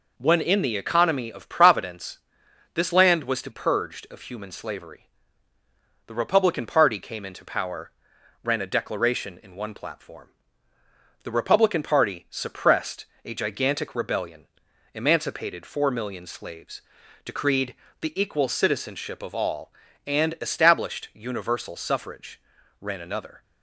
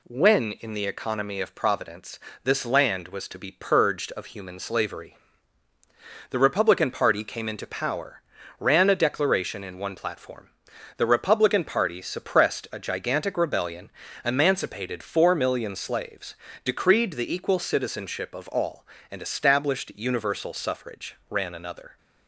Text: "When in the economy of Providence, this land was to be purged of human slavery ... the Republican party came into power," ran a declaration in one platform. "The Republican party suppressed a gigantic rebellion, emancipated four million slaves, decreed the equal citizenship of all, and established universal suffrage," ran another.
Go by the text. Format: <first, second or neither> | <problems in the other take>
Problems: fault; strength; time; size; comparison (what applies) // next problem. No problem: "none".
second | skips "be"; at 3.4 s // pauses between "suppressed" and "a"; slight; at 13.0 s; 0.18 s long // pauses between "decreed" and "the"; slight; at 17.7 s; 0.28 s long